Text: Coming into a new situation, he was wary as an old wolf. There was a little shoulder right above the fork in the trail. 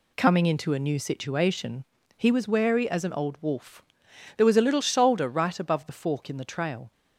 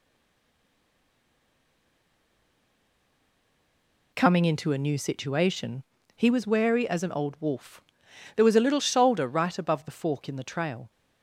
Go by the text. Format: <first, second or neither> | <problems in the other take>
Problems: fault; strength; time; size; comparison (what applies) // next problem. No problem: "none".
first | stays silent before the first word; strong; until 4.1 s; 4.1 s long